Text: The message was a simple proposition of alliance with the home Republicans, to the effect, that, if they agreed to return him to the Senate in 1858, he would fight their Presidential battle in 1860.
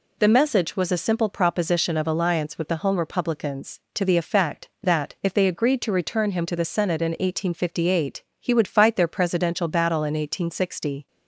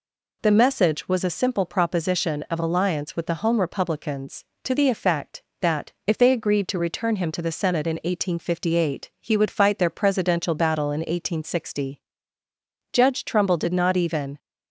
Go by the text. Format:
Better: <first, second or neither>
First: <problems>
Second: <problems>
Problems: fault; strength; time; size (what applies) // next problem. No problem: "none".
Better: first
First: none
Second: goes on to say "Judge Trumbull did not even"; from 12.9 s on; 1.4 s long